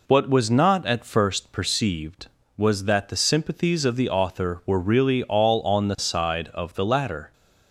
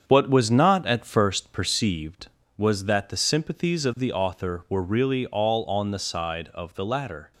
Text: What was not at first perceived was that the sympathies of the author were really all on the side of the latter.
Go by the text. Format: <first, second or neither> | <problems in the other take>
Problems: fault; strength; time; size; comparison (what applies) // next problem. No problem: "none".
first | gets quieter; noticeable; throughout; 5.5 dB